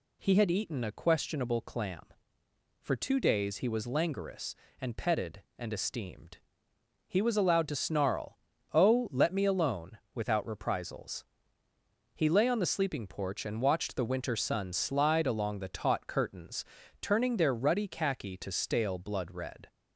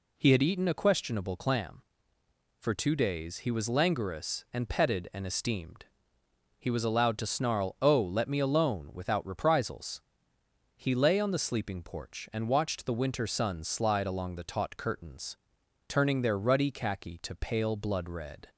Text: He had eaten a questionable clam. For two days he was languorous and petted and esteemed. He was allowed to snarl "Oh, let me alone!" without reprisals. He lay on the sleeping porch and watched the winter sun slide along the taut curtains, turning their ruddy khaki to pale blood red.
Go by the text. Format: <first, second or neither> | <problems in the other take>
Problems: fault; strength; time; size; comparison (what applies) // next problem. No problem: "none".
second | pauses between "snarl" and "Oh"; slight; at 8.3 s; 0.36 s long // says "stale" for "pale"; at 18.5 s